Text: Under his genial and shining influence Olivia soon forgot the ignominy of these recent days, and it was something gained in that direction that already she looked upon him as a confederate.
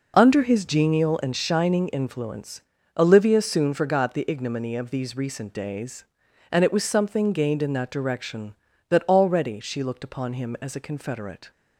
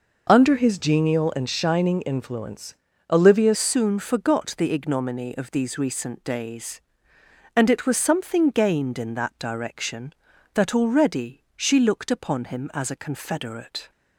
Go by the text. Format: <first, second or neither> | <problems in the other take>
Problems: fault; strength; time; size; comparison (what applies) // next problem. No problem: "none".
first | pauses between "influence" and "Olivia"; slight; at 2.7 s; 0.36 s long; slight in the first // changes voice at "soon"; from 3.5 s on; 10.4 s long